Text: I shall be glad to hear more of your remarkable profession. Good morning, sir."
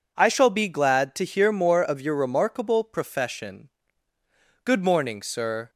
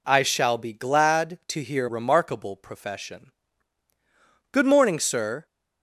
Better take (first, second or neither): first